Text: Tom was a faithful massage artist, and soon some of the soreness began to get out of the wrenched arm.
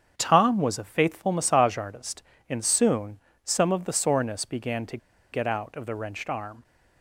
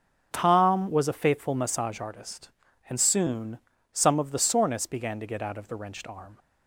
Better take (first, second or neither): second